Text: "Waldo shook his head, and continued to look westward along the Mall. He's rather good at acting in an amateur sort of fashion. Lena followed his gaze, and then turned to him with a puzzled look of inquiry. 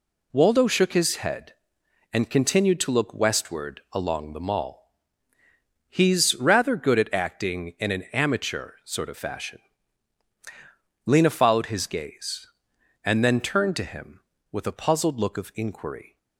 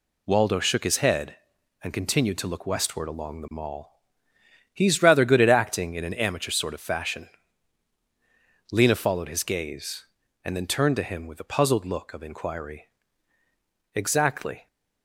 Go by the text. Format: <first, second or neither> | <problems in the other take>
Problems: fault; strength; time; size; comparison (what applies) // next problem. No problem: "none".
first | goes on to say "Exactly"; noticeable; from 13.9 s on; 0.72 s long